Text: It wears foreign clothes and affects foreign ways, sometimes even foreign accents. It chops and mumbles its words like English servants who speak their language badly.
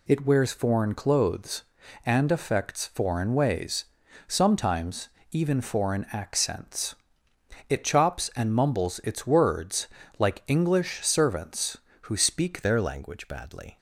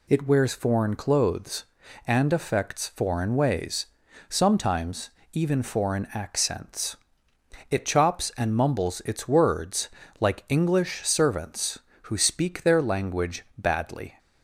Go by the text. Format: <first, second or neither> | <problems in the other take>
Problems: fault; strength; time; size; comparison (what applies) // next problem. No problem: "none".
second | pauses between "sometimes" and "even"; slight; at 5.0 s; 0.22 s long; slight in the second // pauses between "words" and "like"; slight; at 9.8 s; 0.30 s long; slight in the second // changes voice at "their"; from 12.6 s on; 1.1 s long